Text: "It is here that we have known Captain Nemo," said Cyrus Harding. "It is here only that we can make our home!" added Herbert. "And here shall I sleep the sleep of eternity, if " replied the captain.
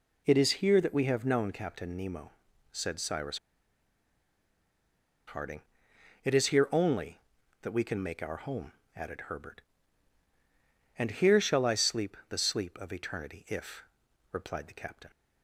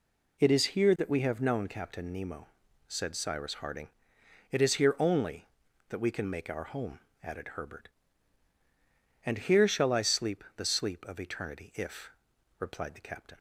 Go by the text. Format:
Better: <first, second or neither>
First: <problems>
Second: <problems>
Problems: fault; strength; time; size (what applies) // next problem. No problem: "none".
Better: second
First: pauses between "Cyrus" and "Harding"; strong; at 3.3 s; 1.8 s long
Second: none